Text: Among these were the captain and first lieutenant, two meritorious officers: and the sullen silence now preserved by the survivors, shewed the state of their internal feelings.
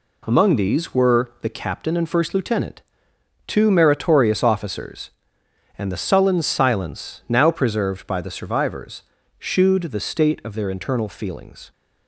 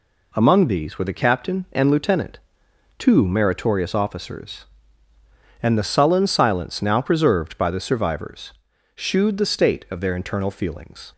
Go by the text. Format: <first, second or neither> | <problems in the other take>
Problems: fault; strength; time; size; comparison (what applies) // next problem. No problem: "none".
first | skips "first"; at 1.8 s